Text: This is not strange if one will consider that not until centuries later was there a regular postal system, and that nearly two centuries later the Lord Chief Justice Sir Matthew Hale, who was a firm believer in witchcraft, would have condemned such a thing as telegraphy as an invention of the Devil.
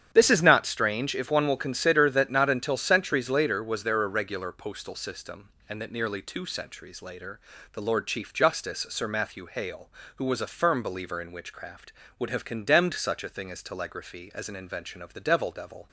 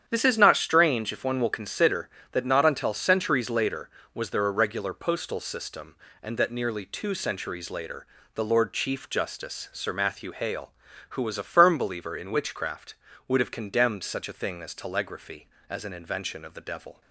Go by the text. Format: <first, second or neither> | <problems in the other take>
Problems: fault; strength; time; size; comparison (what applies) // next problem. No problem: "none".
second | starts louder than the rest; strong; until 1.1 s; 9 dB; strong in the second // pauses between "later" and "the"; slight; at 7.3 s; 0.34 s long; slight in the second // says "Devil" twice; at 15.5 s